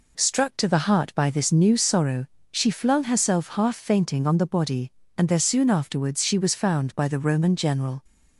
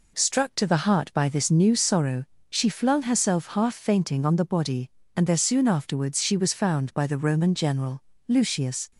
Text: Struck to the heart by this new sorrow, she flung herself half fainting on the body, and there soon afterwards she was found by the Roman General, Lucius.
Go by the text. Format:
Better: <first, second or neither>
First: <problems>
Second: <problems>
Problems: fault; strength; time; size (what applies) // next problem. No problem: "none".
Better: second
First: stops before "Lucius"; at 8.0 s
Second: none